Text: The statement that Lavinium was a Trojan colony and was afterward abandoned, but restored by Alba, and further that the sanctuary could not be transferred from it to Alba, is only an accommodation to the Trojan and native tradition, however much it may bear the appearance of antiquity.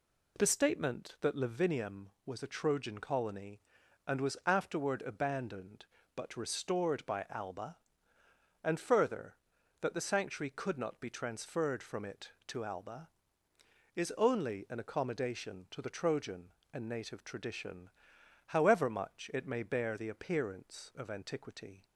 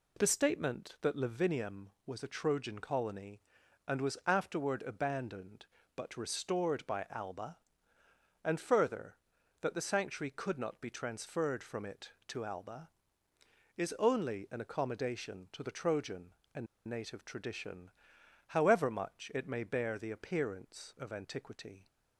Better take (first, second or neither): first